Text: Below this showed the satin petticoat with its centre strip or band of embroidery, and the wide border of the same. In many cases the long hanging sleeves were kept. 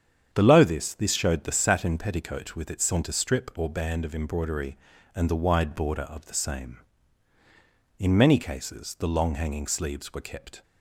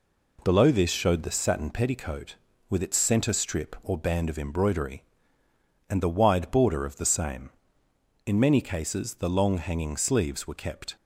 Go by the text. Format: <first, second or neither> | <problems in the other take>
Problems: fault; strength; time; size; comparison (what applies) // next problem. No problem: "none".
second | starts louder than the rest; strong; until 1.3 s; 8 dB // says "this" twice; at 0.9 s